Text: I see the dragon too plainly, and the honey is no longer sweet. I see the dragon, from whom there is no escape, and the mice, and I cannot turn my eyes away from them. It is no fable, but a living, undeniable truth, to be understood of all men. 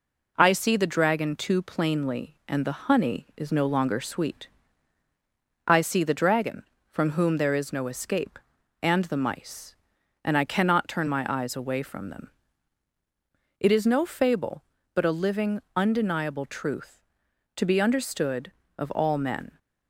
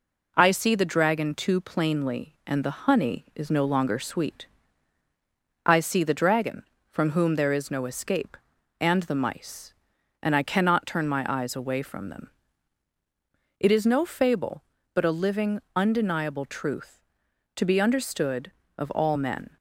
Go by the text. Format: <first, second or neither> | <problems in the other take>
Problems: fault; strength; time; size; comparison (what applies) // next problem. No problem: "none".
neither | none